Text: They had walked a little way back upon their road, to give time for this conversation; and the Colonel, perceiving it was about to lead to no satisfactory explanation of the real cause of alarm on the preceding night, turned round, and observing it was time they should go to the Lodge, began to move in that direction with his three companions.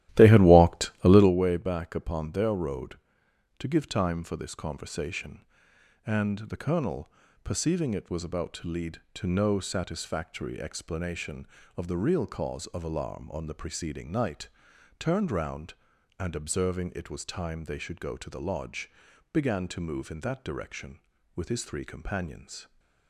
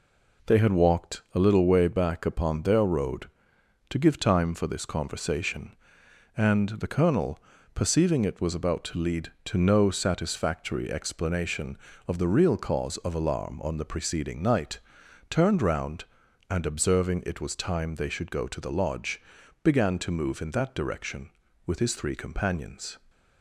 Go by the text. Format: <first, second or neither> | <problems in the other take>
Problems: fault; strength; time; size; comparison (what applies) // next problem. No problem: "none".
second | starts louder than the rest; strong; until 1.4 s; 14 dB